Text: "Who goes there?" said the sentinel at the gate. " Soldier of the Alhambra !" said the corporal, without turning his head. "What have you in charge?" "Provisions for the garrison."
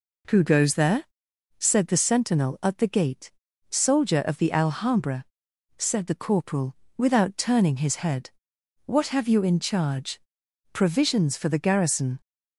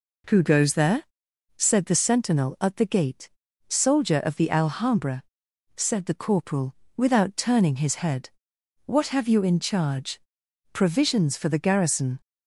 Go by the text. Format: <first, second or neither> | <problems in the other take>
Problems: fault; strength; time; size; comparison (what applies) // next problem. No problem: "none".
neither | none